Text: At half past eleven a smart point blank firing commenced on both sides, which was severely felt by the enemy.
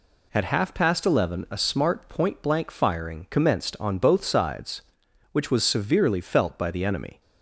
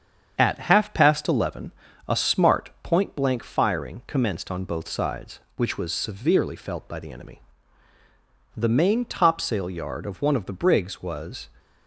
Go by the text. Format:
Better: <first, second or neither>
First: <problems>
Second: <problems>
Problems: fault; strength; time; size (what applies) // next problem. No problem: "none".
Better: first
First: none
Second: starts louder than the rest; strong; until 1.3 s; 7.5 dB // pauses between "eleven" and "a"; slight; at 1.7 s; 0.36 s long // goes on to say "The main topsail yard of one of the brigs was"; strong; from 8.5 s on; 2.9 s long